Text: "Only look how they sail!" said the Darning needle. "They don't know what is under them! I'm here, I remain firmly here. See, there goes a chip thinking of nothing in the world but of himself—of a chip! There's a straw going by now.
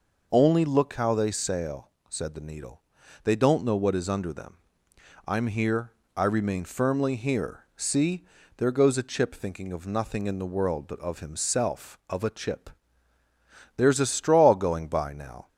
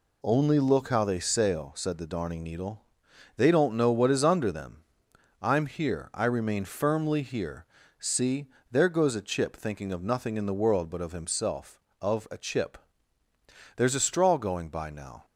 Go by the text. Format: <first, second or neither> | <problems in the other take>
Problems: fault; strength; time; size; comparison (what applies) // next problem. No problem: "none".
second | skips "Darning"; at 2.4 s